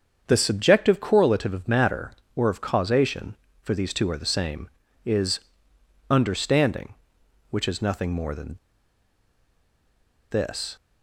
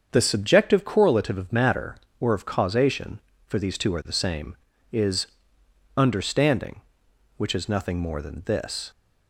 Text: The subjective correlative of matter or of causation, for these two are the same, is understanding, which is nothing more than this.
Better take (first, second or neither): second